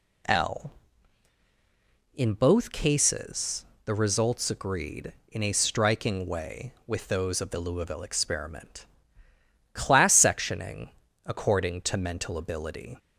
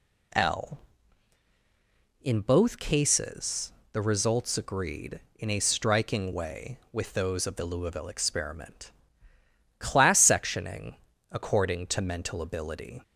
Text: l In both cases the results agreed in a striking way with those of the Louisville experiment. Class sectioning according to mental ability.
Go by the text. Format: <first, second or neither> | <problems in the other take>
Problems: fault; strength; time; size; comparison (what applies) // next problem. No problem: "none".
neither | pauses between "cases" and "the"; slight; the same in both // pauses between "sectioning" and "according"; slight; the same in both